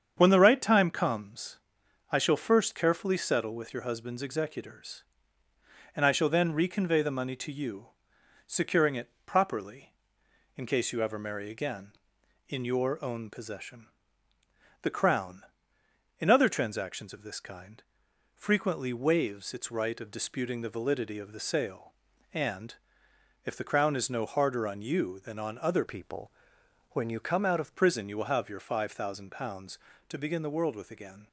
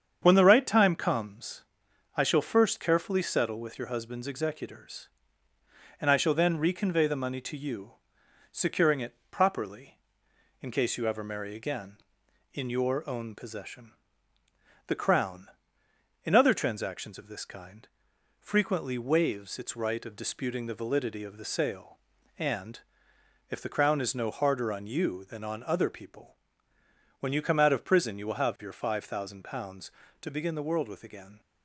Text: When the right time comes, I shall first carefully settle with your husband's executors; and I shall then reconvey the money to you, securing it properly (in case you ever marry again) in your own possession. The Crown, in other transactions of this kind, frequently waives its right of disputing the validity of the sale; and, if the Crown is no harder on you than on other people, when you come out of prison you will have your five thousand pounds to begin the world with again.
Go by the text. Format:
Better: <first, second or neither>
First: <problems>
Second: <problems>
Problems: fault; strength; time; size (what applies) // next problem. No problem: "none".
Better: second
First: starts louder than the rest; strong; until 1.1 s; 8 dB // changes voice from "people" to "of"; from 25.8 to 27.7 s; 1.9 s long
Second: starts louder than the rest; strong; until 1.2 s; 8 dB